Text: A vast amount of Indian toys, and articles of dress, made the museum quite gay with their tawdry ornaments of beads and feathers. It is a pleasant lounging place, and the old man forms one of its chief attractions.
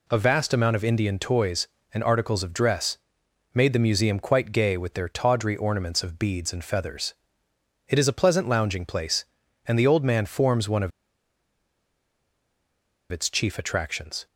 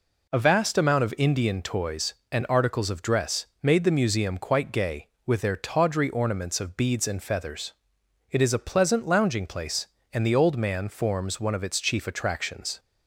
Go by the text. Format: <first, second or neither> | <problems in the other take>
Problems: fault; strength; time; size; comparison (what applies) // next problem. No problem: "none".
second | pauses between "of" and "its"; strong; at 10.9 s; 2.2 s long